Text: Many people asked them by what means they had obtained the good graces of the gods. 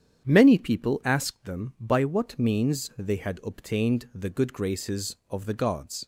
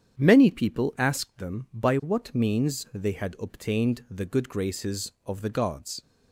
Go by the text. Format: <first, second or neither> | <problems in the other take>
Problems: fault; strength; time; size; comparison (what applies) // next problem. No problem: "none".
neither | starts louder than the rest; strong; the same in both